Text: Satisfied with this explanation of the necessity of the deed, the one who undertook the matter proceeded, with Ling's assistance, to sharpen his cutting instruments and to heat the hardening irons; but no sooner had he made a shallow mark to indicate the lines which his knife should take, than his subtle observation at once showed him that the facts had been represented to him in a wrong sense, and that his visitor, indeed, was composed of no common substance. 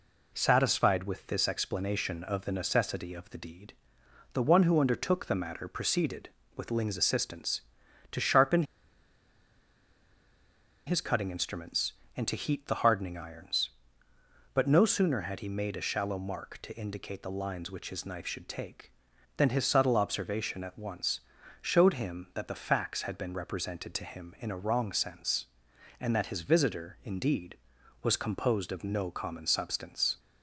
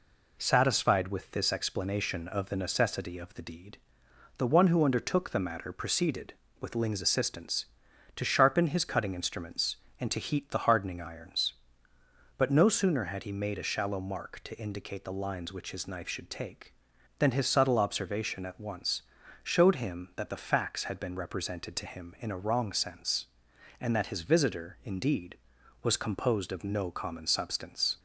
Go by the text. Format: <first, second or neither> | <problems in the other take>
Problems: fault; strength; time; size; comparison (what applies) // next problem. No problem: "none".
second | pauses between "sharpen" and "his"; strong; at 8.6 s; 2.2 s long // pauses between "once" and "showed"; at 21.1 s; 0.42 s long; also in the second